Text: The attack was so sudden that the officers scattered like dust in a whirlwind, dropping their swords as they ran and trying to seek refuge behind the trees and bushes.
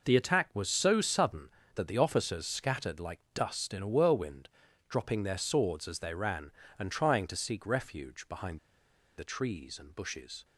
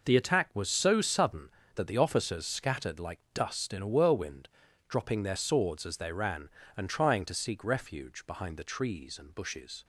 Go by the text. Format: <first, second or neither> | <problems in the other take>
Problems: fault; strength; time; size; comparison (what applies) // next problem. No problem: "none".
second | pauses between "behind" and "the"; noticeable; at 8.5 s; 0.59 s long